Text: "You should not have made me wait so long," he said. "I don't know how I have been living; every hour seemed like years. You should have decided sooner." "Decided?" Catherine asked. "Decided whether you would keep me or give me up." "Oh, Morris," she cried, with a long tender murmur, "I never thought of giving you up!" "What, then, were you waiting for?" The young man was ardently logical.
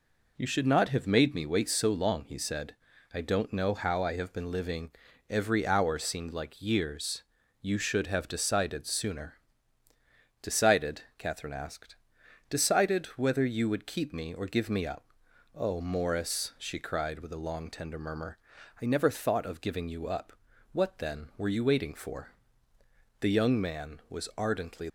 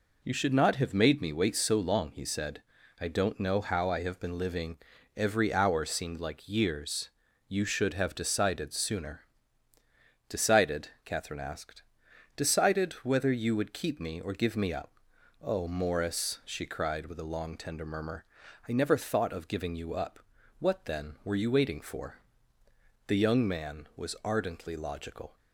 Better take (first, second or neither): second